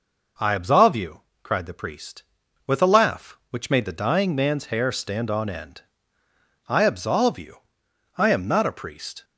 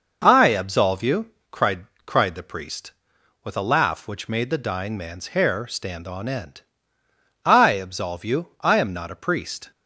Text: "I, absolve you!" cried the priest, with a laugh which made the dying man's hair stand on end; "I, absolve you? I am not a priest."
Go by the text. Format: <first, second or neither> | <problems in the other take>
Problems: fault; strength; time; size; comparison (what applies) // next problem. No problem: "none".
first | says "cried" twice; at 2.0 s